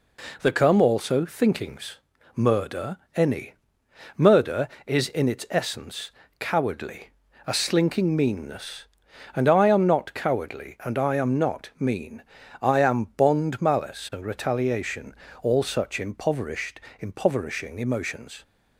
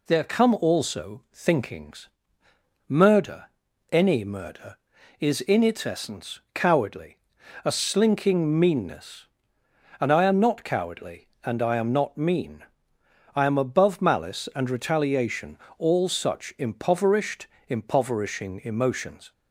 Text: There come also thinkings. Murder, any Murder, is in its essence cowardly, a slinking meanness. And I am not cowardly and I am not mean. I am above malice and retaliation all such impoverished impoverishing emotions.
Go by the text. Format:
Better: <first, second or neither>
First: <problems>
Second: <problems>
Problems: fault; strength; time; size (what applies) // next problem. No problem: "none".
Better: second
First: pauses between "any" and "Murder"; noticeable; at 3.5 s; 0.62 s long // pauses between "essence" and "cowardly"; slight; at 6.0 s; 0.30 s long // says "bond" for "above"; at 13.1 s // pauses between "retaliation" and "all"; slight; at 15.1 s; 0.30 s long // pauses between "impoverished" and "impoverishing"; slight; at 16.8 s; 0.18 s long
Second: pauses between "retaliation" and "all"; slight; at 15.5 s; 0.20 s long // pauses between "impoverished" and "impoverishing"; slight; at 17.4 s; 0.22 s long